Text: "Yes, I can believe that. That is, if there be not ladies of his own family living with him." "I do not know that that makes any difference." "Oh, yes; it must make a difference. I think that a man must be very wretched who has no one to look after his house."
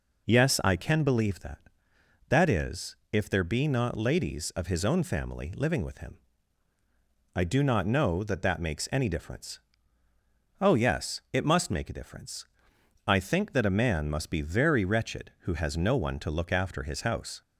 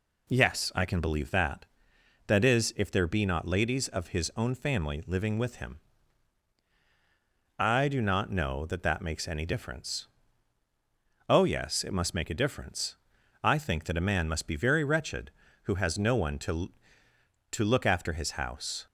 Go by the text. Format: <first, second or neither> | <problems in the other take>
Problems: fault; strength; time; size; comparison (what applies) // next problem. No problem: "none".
first | says "to" twice; at 17.5 s